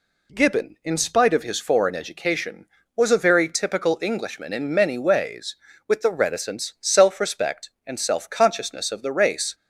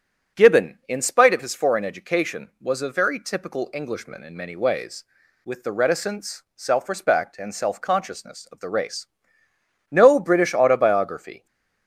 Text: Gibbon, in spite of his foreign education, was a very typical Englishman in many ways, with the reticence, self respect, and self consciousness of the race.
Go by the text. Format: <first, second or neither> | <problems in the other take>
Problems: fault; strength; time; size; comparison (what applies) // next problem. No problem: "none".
first | starts louder than the rest; strong; until 1.4 s; 7.5 dB // goes on to say "No British autobiography"; from 9.8 s on; 1.5 s long // stays silent after the last word; slight; from 11.3 s on; 0.5 s long